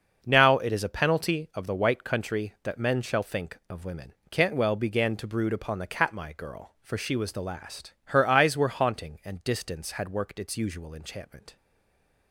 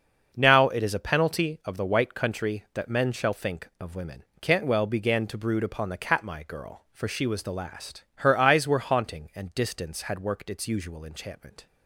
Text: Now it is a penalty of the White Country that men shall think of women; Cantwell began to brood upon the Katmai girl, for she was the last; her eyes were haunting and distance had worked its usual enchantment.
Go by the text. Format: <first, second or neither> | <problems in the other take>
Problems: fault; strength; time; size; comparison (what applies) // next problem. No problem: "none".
second | starts louder than the rest; until 1.2 s; 6 dB; also in the second // stays silent after the last word; slight; from 11.5 s on; 0.8 s long